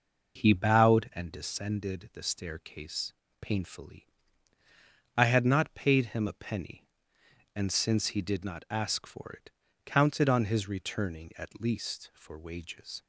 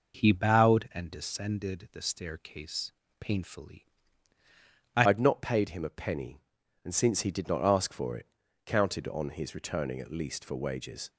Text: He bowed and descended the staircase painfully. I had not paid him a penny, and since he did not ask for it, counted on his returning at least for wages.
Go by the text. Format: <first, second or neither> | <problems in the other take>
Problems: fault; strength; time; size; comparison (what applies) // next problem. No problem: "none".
first | pauses between "staircase" and "painfully"; slight; at 2.9 s; 0.26 s long; slight in the first // changes voice at "had"; from 5.0 s on; 6.0 s long